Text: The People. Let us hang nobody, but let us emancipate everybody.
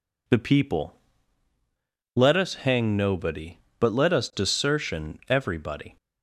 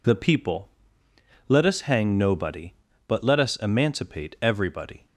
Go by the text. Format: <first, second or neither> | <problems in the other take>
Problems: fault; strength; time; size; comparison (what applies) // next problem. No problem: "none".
second | says "desertion" for "emancipate"; at 4.3 s